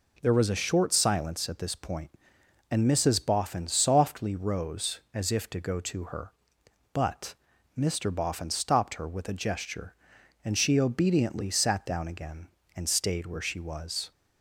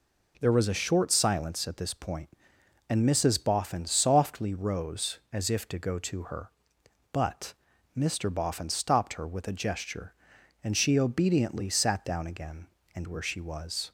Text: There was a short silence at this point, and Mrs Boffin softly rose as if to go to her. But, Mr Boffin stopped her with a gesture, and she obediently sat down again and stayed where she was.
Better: first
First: none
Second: skips "stayed"; at 13.0 s

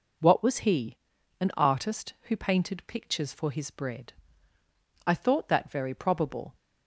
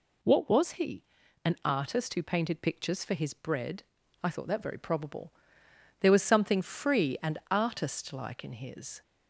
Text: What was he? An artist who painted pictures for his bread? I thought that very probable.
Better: first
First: none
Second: goes on to say "There was something free and artist like in his"; strong; from 6.0 s on; 3.0 s long

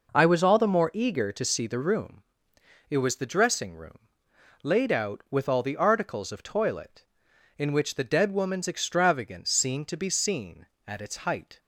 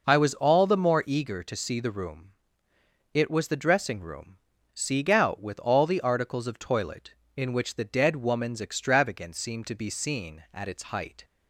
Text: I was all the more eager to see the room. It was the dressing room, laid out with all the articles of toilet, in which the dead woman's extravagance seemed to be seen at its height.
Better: first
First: none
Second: says "sieg" for "laid"; at 4.7 s

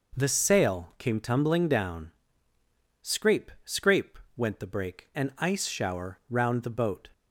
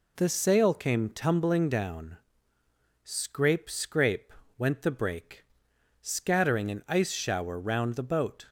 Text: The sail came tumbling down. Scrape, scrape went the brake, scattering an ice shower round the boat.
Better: second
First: pauses between "scrape" and "went"; slight; at 4.1 s; 0.20 s long // skips "scattering"; at 5.1 s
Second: pauses between "scrape" and "went"; slight; at 4.3 s; 0.26 s long

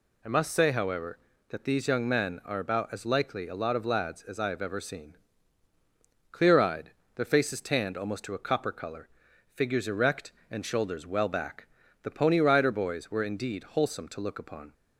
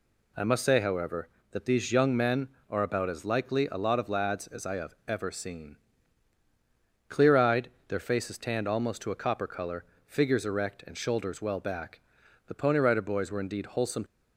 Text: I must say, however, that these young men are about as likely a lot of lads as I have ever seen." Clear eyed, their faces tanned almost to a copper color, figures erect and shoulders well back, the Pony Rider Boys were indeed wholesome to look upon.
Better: first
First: none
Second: stops before "to look upon"; at 14.0 s

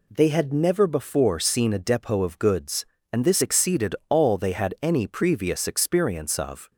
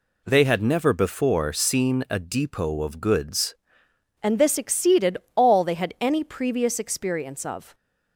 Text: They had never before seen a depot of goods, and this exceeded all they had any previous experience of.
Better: first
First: none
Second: changes voice at "and"; from 4.2 s on; 3.5 s long // pauses between "exceeded" and "all"; slight; at 5.1 s; 0.20 s long

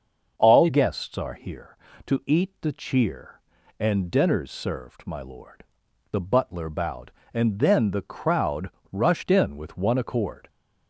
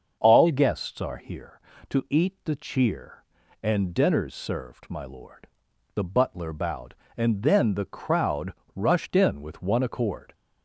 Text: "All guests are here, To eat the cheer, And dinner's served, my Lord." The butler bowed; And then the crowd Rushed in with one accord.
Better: neither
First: starts louder than the rest; until 1.3 s; 6.5 dB // pauses between "crowd" and "Rushed"; slight; at 8.7 s; 0.22 s long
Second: starts louder than the rest; until 1.2 s; 6.5 dB // pauses between "crowd" and "Rushed"; slight; at 8.5 s; 0.22 s long

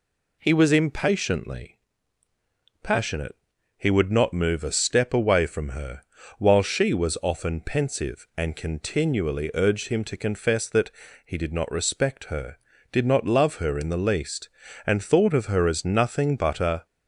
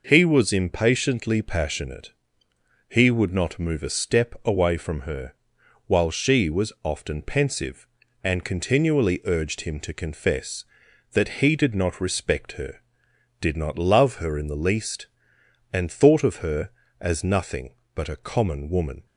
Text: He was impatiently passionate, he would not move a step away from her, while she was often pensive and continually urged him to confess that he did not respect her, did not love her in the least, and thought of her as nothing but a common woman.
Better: second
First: pauses between "impatiently" and "passionate"; at 1.7 s; 1.0 s long // pauses between "that" and "he"; slight; at 10.9 s; 0.34 s long // stops before "common woman"; at 16.8 s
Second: none

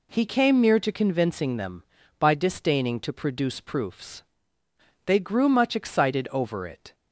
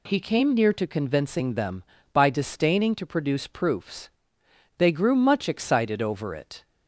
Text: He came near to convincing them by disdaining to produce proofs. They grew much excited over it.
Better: neither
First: none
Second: none

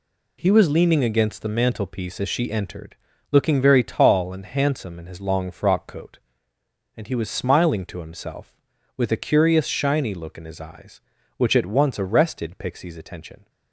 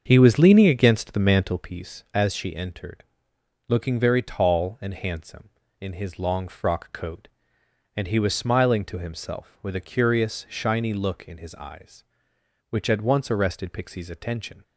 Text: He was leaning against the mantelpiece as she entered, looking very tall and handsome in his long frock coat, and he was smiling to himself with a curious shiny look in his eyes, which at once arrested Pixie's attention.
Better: first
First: none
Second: starts louder than the rest; until 1.7 s; 7 dB

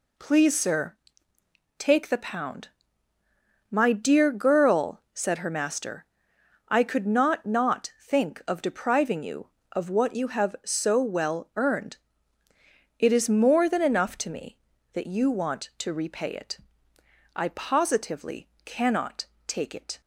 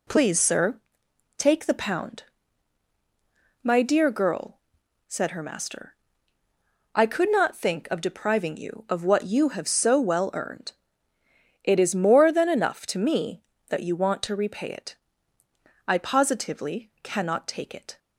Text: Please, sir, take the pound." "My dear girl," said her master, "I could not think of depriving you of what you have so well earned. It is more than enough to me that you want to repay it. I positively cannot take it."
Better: second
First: says "not" twice; at 7.4 s // pauses between "positively" and "cannot"; slight; at 18.4 s; 0.16 s long // pauses between "cannot" and "take"; slight; at 19.2 s; 0.20 s long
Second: none

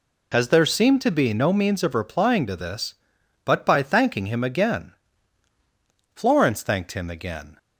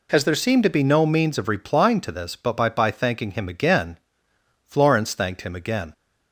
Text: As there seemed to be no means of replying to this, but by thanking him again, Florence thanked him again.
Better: first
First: none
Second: says "by" twice; at 2.6 s

